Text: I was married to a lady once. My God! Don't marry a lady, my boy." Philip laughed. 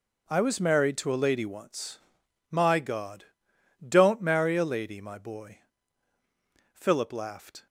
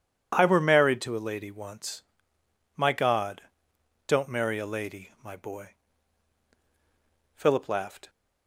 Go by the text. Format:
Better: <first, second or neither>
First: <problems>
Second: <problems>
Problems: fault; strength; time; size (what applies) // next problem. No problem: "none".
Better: first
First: none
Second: says "were" for "was"; at 0.4 s